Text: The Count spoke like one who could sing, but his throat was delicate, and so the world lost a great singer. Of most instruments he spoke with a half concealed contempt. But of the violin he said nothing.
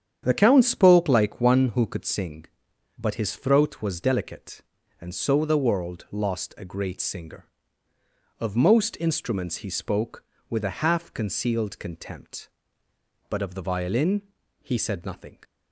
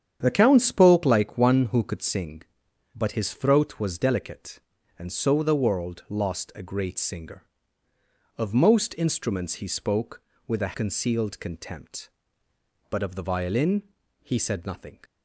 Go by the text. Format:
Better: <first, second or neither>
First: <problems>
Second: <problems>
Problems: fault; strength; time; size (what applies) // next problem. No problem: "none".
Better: first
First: starts louder than the rest; strong; until 1.2 s; 8.5 dB // pauses between "violin" and "he"; at 14.2 s; 0.40 s long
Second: starts louder than the rest; strong; until 1.2 s; 8.5 dB // skips "half"; at 10.7 s // pauses between "violin" and "he"; at 13.8 s; 0.40 s long